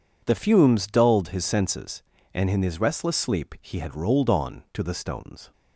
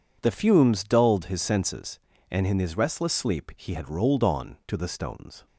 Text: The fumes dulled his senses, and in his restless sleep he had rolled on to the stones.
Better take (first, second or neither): neither